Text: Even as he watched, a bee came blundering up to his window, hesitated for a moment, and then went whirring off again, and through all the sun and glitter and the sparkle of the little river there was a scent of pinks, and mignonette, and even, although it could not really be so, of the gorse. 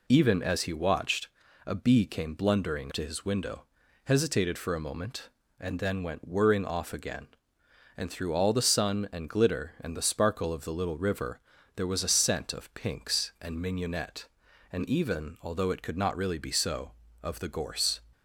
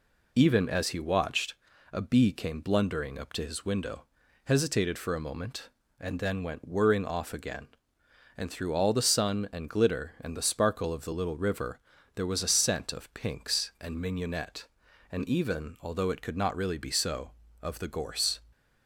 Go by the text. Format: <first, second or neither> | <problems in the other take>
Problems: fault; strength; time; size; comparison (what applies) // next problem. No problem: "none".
second | skips "up"; at 2.9 s // pauses between "river" and "there"; slight; at 11.4 s; 0.34 s long; slight in the second